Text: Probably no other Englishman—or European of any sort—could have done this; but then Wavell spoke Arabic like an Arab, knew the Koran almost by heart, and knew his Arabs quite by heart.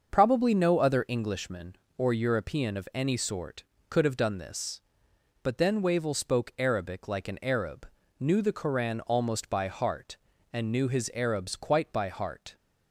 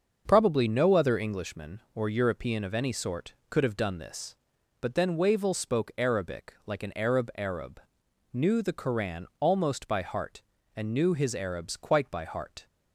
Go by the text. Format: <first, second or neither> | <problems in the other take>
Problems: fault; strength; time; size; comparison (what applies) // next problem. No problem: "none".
first | starts louder than the rest; until 1.2 s; 6.5 dB; also in the first // says "Arab" twice; at 7.3 s